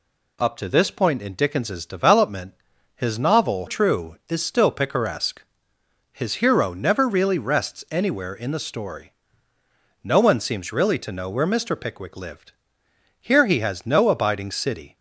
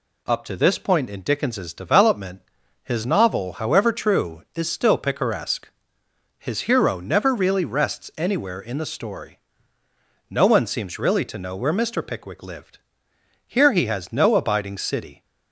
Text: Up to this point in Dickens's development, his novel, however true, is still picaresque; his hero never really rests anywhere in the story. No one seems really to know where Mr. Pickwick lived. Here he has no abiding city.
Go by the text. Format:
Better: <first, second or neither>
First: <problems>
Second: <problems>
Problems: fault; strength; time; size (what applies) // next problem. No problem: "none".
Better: second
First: skips "however"; at 3.6 s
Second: none